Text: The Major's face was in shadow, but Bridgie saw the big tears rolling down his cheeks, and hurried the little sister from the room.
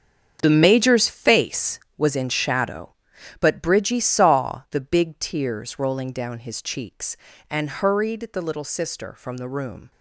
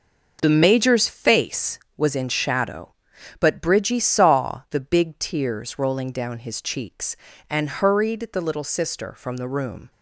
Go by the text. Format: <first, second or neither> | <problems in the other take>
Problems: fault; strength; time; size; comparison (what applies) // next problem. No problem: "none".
second | gets quieter; strong; throughout; 12 dB